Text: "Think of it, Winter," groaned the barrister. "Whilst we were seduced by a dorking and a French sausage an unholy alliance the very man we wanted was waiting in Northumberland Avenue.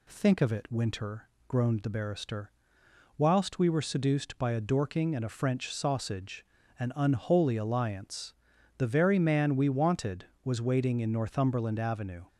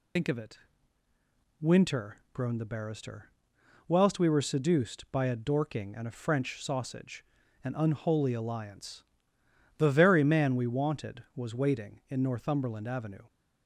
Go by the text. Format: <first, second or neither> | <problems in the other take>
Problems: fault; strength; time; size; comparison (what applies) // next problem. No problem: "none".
first | loses the start of "Think"; at 0.1 s; 90 ms // pauses between "sausage" and "an"; at 7.2 s; 0.40 s long; slight in the first // pauses between "alliance" and "the"; noticeable; at 9.0 s; 0.76 s long; noticeable in the first